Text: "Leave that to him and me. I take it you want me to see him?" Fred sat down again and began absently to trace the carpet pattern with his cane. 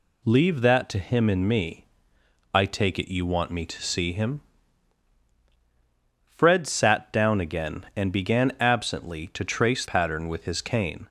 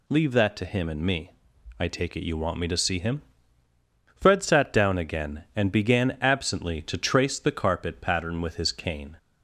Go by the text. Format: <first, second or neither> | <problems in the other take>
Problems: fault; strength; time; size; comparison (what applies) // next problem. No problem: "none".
second | skips "the carpet"; at 9.8 s